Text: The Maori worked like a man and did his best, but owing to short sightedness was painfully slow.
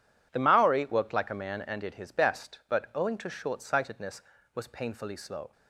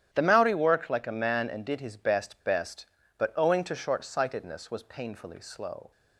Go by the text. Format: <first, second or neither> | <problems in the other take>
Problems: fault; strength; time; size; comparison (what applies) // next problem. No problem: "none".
first | starts louder than the rest; strong; until 1.1 s; 10.5 dB // says "best" twice; at 2.4 s